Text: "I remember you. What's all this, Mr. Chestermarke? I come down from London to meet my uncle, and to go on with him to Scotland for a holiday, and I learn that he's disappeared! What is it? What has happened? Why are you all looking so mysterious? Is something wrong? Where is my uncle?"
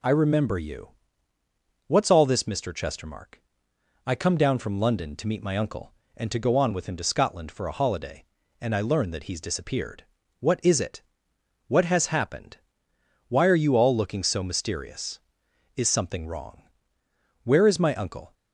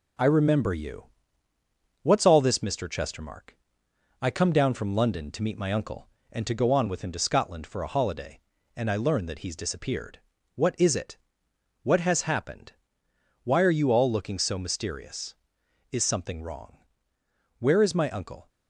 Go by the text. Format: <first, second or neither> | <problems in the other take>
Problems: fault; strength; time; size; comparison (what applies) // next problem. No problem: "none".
first | gets quieter; throughout; 3.5 dB